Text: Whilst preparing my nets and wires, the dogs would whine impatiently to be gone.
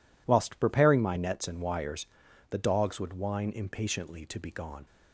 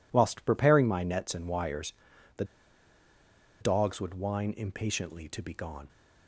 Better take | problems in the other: first | pauses between "the" and "dogs"; at 2.4 s; 1.1 s long

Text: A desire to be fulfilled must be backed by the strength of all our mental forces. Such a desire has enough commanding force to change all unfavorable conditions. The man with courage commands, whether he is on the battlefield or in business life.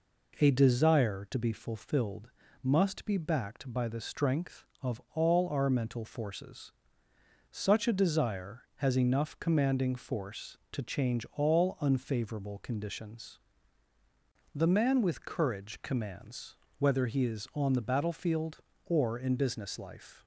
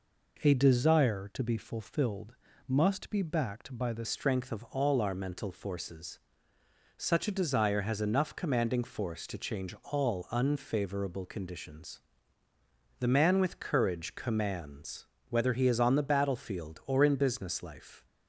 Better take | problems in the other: first | pauses between "fulfilled" and "must"; slight; at 2.3 s; 0.32 s long; slight in the first // changes voice at "strength"; from 4.0 s on; 14.0 s long

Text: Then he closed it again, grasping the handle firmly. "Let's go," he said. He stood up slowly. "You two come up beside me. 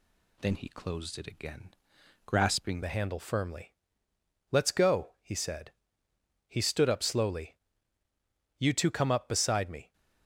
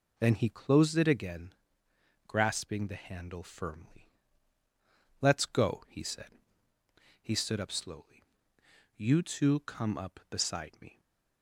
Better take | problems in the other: second | changes voice at "the"; from 2.8 s on; 7.1 s long

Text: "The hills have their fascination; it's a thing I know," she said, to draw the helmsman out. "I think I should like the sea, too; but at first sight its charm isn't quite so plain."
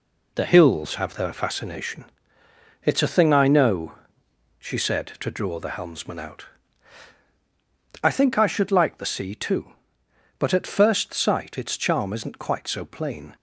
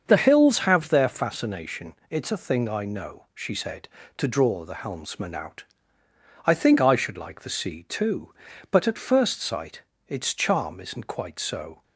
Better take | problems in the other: first | starts louder than the rest; until 1.0 s; 6.5 dB // pauses between "sight" and "its"; slight; at 9.8 s; 0.26 s long // stops before "plain"; at 11.8 s

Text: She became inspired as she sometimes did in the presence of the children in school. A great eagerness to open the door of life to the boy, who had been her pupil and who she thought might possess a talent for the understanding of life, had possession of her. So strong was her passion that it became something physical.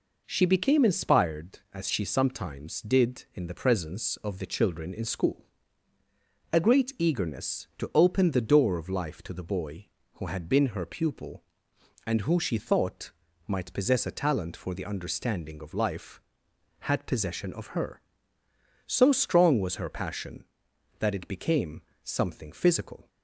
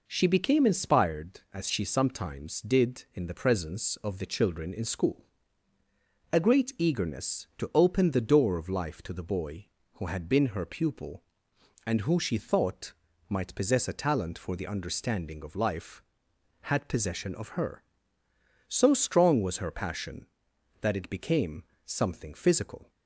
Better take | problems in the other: neither | pauses between "thought" and "might"; slight; the same in both // pauses between "became" and "something"; slight; the same in both

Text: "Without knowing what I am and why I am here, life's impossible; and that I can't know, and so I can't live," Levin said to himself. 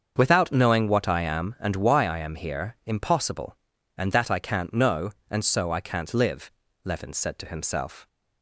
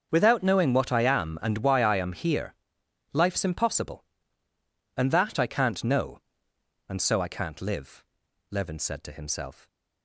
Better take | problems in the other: second | starts louder than the rest; until 1.1 s; 7 dB; also in the second // skips "life's"; at 2.8 s

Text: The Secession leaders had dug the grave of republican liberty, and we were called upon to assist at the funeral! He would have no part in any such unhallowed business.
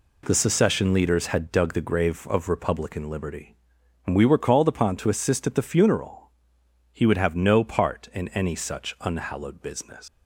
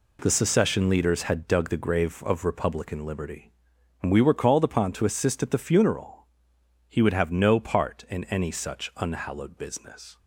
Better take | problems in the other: second | leaves "business" unfinished; at 10.0 s; 140 ms

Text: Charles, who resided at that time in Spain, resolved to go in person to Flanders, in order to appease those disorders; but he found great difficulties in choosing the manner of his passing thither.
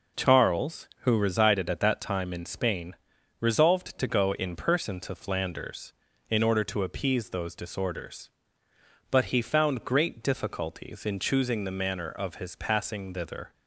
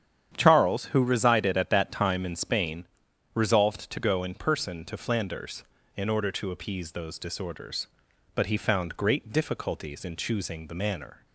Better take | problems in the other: first | starts louder than the rest; strong; until 1.3 s; 9 dB // stops before "of his passing thither"; at 11.2 s

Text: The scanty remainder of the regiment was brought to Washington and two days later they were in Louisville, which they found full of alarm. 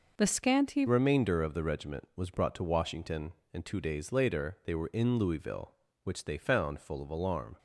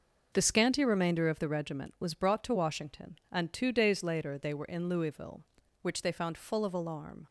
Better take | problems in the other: second | changes voice at "remainder"; from 0.8 s on; 6.7 s long

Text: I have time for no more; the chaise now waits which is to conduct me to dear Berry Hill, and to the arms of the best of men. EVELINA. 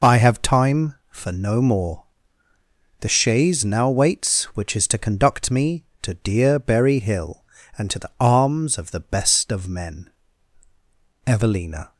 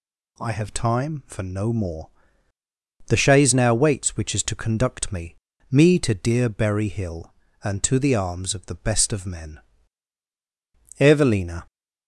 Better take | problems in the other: first | says "me" twice; at 5.6 s

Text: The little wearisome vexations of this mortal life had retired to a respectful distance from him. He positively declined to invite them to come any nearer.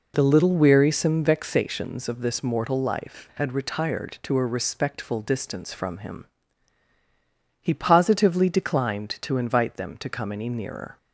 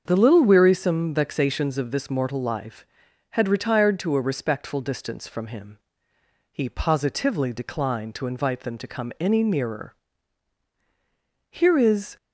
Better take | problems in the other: first | starts louder than the rest; until 1.0 s; 7 dB // goes on to say "Here is"; noticeable; from 11.5 s on; 0.66 s long

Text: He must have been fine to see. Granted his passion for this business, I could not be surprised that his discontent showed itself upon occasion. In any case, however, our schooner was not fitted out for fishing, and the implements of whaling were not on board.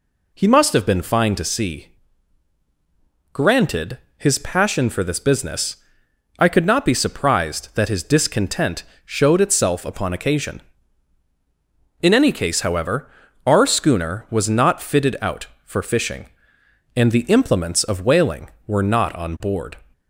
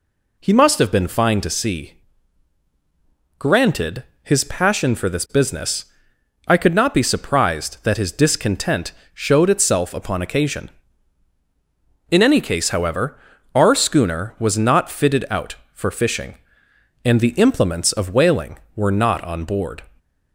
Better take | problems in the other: neither | pauses between "Granted" and "his"; slight; the same in both // pauses between "discontent" and "showed"; slight; the same in both

